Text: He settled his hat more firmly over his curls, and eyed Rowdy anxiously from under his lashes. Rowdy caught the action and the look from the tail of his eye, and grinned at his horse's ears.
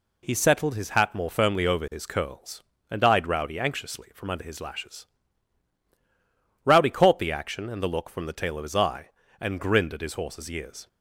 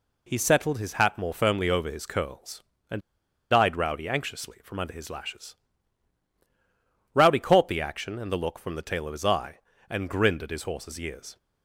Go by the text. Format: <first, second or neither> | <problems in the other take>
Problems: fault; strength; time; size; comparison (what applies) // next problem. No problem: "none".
first | pauses between "and" and "eyed"; noticeable; at 3.0 s; 0.49 s long